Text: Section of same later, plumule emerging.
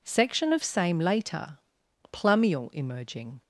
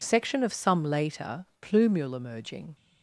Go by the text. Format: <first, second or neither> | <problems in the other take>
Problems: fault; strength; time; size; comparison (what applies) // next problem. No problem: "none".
first | says "some" for "same"; at 0.5 s